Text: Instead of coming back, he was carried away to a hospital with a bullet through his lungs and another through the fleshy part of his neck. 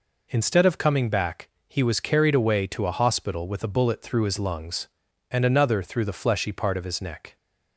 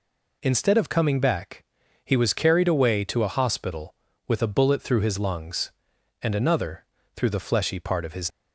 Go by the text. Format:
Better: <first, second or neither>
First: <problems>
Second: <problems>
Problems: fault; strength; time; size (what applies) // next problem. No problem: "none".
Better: first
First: none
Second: pauses between "another" and "through"; slight; at 6.8 s; 0.32 s long // stops before "neck"; at 8.2 s